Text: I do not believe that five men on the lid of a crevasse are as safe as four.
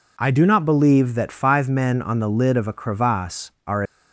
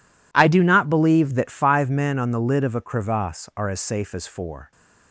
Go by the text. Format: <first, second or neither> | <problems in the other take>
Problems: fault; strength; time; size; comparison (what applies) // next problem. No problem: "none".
second | stops before "as safe as four"; at 3.8 s